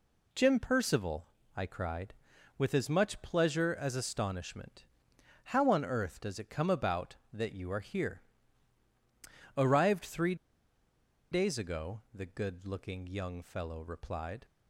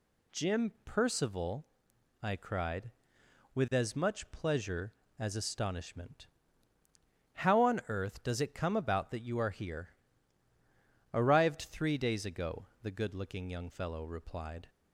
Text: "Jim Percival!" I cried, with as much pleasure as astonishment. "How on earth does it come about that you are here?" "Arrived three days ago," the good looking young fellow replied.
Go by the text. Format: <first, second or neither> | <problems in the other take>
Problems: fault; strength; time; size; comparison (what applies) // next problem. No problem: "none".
second | pauses between "three" and "days"; noticeable; at 10.3 s; 0.96 s long